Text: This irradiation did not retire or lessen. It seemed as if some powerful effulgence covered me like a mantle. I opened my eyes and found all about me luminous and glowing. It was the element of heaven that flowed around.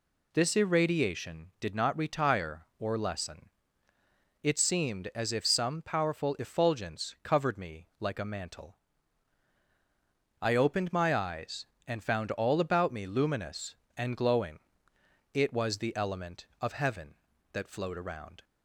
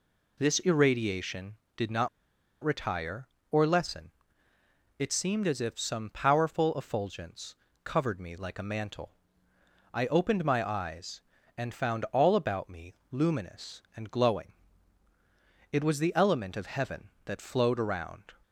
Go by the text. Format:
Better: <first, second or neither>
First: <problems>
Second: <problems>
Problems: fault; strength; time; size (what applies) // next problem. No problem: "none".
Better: first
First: none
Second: pauses between "not" and "retire"; noticeable; at 2.0 s; 0.55 s long // pauses between "effulgence" and "covered"; slight; at 7.5 s; 0.30 s long // pauses between "me" and "luminous"; slight; at 12.9 s; 0.16 s long